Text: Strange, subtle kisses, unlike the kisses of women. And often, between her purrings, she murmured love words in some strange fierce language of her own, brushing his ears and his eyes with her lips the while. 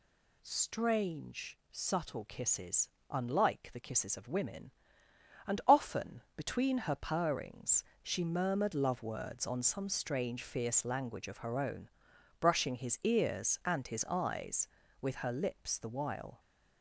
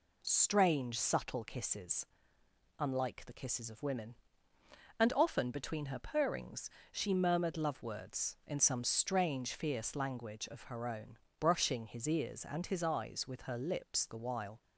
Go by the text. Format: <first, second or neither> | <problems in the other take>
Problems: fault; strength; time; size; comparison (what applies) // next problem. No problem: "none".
second | says "on" for "in"; at 9.4 s